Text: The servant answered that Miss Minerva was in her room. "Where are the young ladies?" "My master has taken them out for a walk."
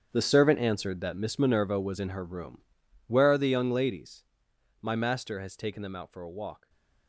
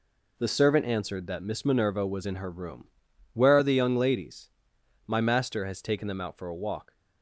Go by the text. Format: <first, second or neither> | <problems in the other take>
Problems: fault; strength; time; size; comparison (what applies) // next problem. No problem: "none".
second | gets quieter; strong; throughout; 14.5 dB // stays silent after the last word; slight; from 6.5 s on; 0.5 s long